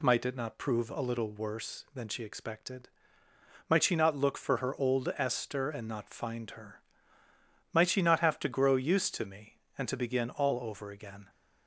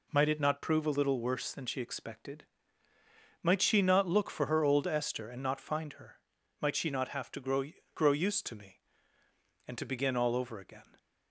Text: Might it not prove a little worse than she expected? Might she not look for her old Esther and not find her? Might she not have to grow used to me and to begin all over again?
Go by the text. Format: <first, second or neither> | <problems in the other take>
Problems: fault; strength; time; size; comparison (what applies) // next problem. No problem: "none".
first | says "grow" twice; at 7.9 s